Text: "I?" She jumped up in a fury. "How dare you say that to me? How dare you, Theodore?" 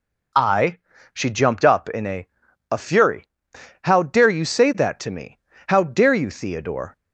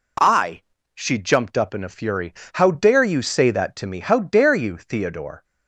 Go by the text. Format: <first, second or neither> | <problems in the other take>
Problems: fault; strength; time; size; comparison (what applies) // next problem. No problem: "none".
second | says "a" twice; at 2.7 s